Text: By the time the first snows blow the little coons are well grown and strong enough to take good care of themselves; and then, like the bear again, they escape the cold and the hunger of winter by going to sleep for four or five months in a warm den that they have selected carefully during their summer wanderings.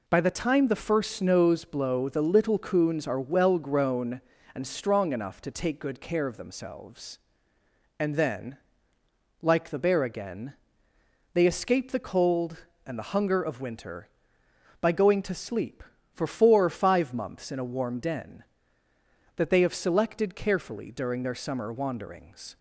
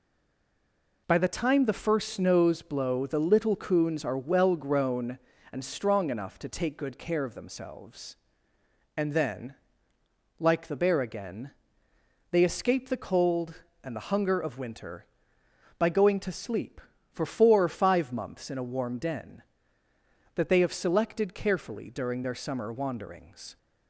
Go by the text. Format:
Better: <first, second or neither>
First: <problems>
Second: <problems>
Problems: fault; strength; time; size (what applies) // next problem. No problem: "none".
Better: first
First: none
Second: stays silent before the first word; until 1.0 s; 1.0 s long